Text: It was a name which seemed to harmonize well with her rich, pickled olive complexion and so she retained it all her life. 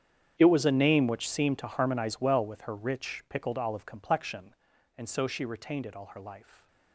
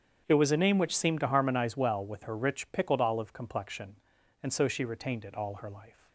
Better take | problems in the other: second | gets quieter; strong; throughout; 19 dB // starts louder than the rest; strong; until 1.3 s; 8.5 dB; strong in the second

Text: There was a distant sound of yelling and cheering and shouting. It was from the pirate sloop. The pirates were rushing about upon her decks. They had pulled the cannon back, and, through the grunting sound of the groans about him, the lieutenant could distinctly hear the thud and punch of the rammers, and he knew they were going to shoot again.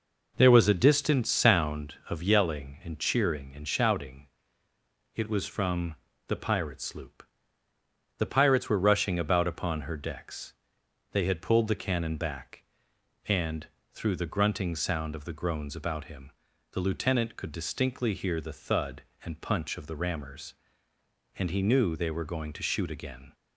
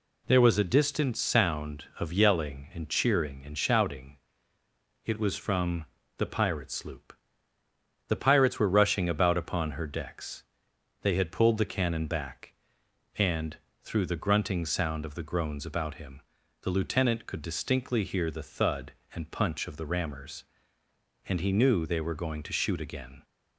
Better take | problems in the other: second | starts louder than the rest; noticeable; until 2.0 s; 5 dB // pauses between "from" and "the"; slight; at 5.9 s; 0.32 s long; slight in the second

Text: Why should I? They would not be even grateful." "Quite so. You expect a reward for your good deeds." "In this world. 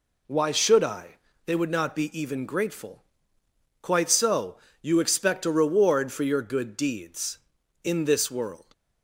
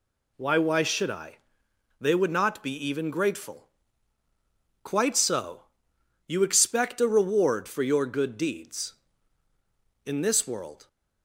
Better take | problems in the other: first | says "Why" twice; at 0.5 s

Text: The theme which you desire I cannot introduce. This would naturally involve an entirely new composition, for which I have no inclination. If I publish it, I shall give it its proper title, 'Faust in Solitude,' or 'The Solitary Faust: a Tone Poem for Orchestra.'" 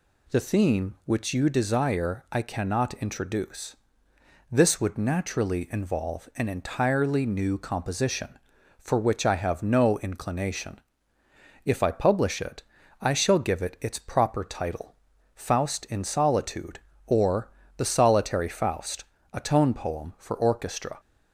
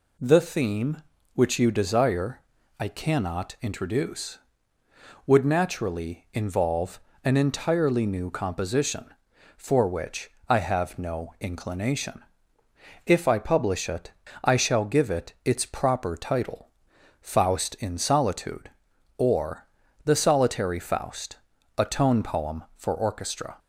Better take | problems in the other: first | pauses between "desire" and "I"; at 2.4 s; 0.38 s long // skips "This"; at 4.8 s // pauses between "involve" and "an"; slight; at 6.9 s; 0.24 s long // pauses between "which" and "I"; slight; at 10.3 s; 0.18 s long // pauses between "or" and "The"; at 19.6 s; 0.40 s long; slight in the first

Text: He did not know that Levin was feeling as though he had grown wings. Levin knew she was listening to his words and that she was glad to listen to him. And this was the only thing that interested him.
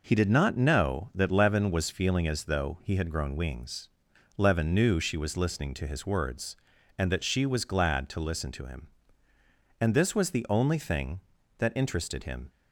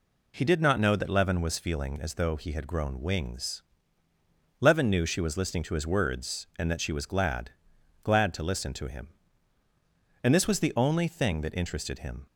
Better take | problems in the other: first | says "glad" twice; at 8.0 s

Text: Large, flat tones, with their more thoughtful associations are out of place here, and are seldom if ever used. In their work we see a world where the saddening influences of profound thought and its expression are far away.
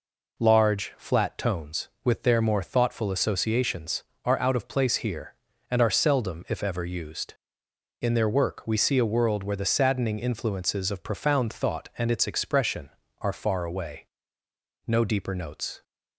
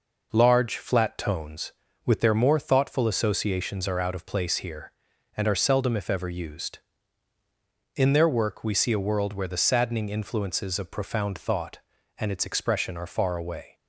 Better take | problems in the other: second | goes on to say "No deeper notes"; noticeable; from 14.8 s on; 0.96 s long

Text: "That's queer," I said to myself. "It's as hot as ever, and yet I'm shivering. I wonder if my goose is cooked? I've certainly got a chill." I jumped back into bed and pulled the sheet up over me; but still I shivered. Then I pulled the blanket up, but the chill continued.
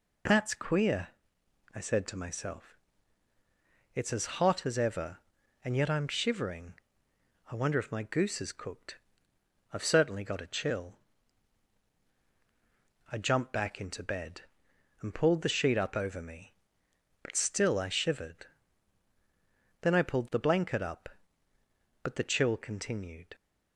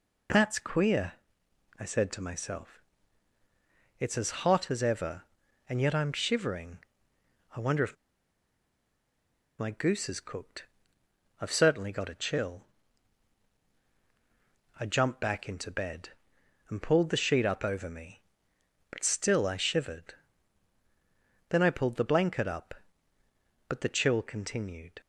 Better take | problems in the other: first | pauses between "as" and "hot"; slight; at 4.3 s; 0.16 s long; slight in the first // pauses between "if" and "my"; strong; at 7.9 s; 1.6 s long

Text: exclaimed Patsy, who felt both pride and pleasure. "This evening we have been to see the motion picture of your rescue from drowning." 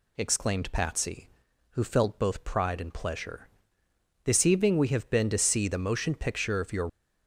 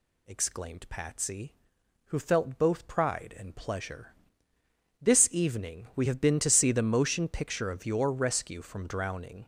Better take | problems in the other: second | stops before "rescue from drowning"; at 6.8 s

